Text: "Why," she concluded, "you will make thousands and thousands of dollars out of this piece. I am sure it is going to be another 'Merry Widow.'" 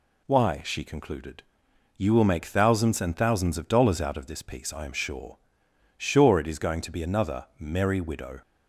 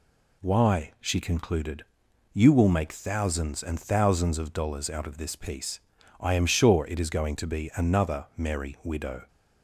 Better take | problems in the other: second | says "sure" twice; at 5.9 s

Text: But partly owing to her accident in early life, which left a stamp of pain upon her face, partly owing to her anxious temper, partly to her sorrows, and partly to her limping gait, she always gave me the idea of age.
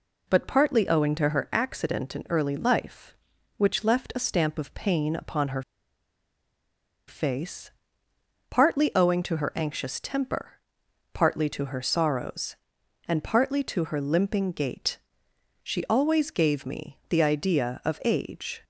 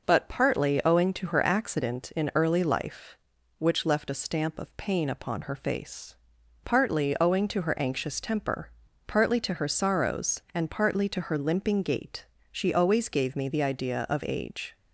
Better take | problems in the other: second | pauses between "her" and "face"; strong; at 5.6 s; 1.4 s long

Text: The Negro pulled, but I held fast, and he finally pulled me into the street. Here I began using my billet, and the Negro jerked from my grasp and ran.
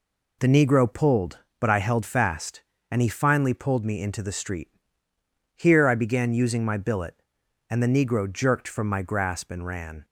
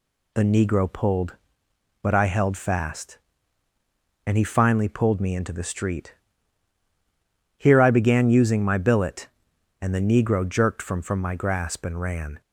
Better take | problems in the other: first | says "from" twice; at 11.0 s

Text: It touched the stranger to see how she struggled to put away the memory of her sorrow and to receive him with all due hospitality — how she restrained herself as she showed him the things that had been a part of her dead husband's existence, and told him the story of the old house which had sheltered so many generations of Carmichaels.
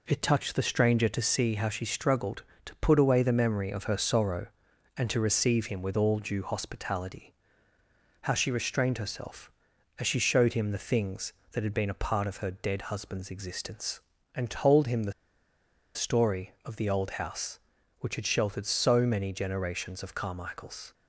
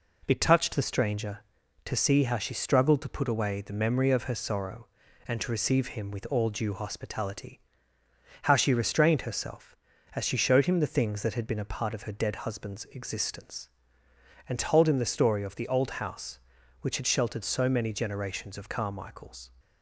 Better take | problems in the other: second | pauses between "the" and "story"; noticeable; at 15.1 s; 0.82 s long

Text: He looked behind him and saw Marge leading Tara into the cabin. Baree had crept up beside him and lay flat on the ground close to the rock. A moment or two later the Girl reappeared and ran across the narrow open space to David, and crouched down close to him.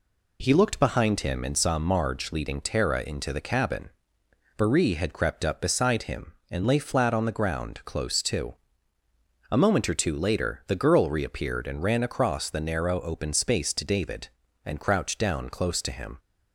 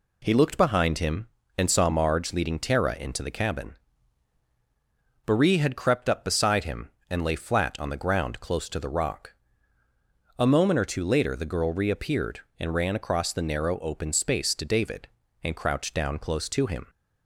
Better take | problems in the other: second | skips "the rock"; at 9.0 s

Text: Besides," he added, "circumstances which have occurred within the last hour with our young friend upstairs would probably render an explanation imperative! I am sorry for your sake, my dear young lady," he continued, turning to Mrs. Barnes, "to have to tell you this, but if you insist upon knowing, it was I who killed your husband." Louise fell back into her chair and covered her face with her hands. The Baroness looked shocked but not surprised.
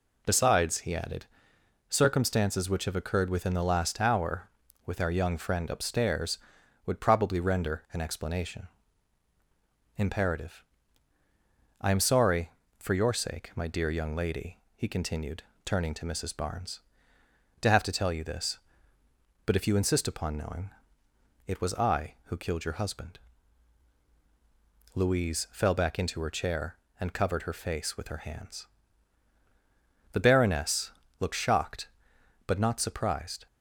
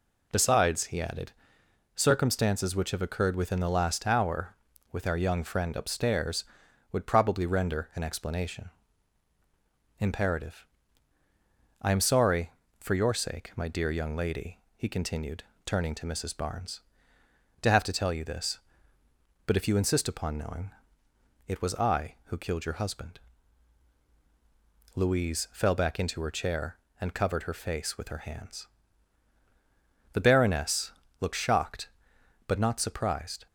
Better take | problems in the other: neither | pauses between "explanation" and "imperative"; strong; the same in both // pauses between "Baroness" and "looked"; slight; the same in both

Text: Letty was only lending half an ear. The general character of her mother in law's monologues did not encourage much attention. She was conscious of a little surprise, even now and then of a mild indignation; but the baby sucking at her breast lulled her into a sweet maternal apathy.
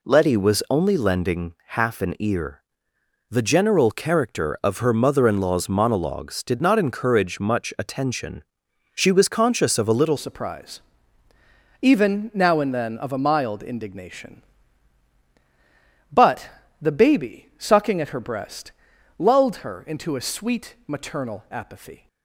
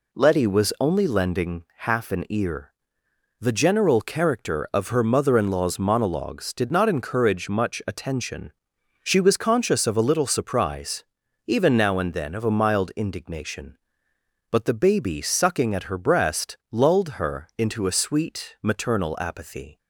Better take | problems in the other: second | changes voice at "surprise"; from 10.1 s on; 11.9 s long // pauses between "but" and "the"; slight; at 16.4 s; 0.34 s long // pauses between "breast" and "lulled"; noticeable; at 18.7 s; 0.48 s long

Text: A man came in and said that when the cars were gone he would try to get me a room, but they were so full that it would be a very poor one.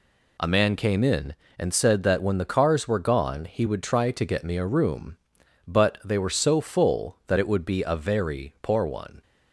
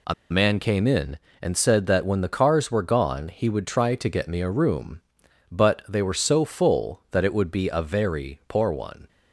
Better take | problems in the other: first | pauses between "A" and "man"; slight; at 0.1 s; 0.17 s long

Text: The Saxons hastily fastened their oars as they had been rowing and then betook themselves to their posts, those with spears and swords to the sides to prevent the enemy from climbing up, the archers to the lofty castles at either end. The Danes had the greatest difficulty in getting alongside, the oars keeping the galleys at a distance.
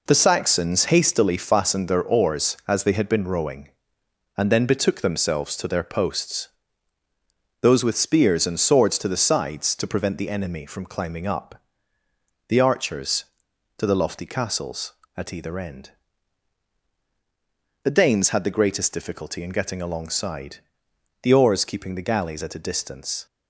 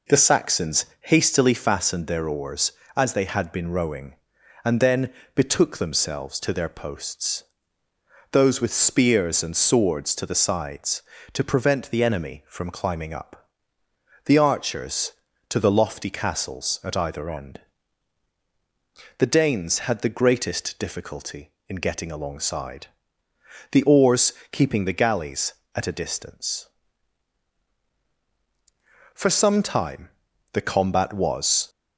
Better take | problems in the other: first | pauses between "Saxons" and "hastily"; slight; at 0.8 s; 0.16 s long // pauses between "then" and "betook"; slight; at 5.1 s; 0.24 s long // pauses between "oars" and "keeping"; slight; at 24.3 s; 0.20 s long // goes on to say "For some time the combat was"; strong; from 29.1 s on; 2.5 s long

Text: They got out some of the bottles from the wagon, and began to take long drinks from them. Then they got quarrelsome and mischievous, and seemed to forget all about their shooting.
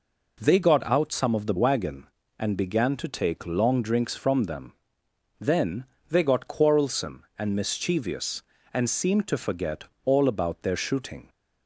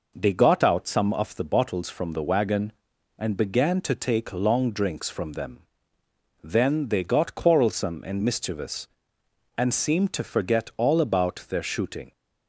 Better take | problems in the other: second | skips "bottles from the"; at 1.5 s // pauses between "Then" and "they"; slight; at 5.8 s; 0.24 s long // pauses between "forget" and "all"; slight; at 9.8 s; 0.22 s long

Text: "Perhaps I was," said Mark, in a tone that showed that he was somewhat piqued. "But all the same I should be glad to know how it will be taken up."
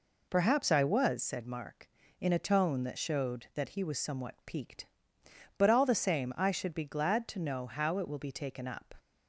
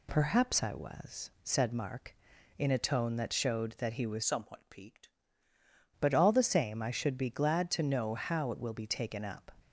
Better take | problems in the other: first | changes voice from "somewhat" to "piqued"; from 4.2 to 5.0 s; 0.8 s long

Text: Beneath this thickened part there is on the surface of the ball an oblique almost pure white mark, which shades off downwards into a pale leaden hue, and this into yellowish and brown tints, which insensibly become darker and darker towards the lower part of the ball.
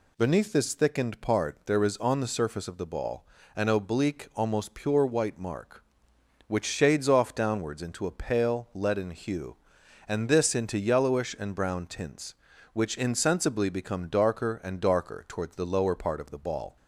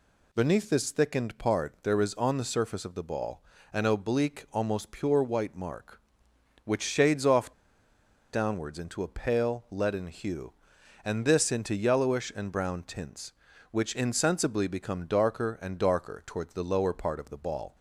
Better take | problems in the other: first | pauses between "ball" and "an"; slight; at 3.4 s; 0.30 s long; slight in the first // pauses between "off" and "downwards"; noticeable; at 7.5 s; 0.81 s long

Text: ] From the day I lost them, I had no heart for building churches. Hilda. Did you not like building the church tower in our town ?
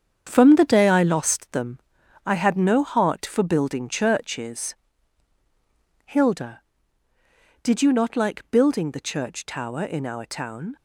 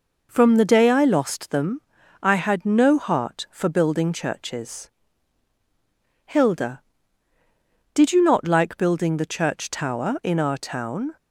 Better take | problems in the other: second | gets quieter; strong; throughout; 8 dB

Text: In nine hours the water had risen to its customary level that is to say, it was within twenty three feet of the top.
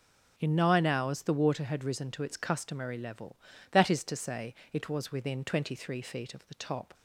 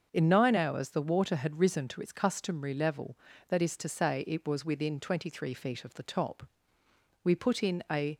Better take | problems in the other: first | starts louder than the rest; until 1.1 s; 6.5 dB // goes on to say "We put in a"; noticeable; from 7.2 s on; 0.94 s long

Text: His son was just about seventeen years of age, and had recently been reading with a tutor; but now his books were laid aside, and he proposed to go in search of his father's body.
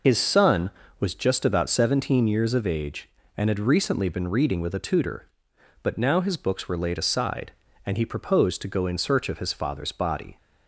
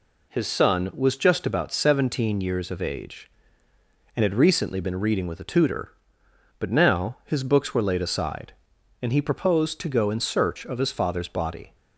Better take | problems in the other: second | loses the start of "His"; at 0.0 s; 60 ms

